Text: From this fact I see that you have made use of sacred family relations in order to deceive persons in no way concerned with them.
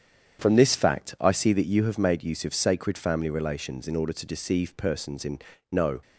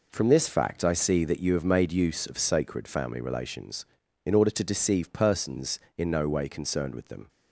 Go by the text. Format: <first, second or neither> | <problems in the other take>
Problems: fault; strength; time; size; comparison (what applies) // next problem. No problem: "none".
second | starts louder than the rest; strong; until 1.4 s; 8.5 dB // pauses between "in" and "no"; slight; at 5.3 s; 0.32 s long // stops before "way concerned with them"; at 6.0 s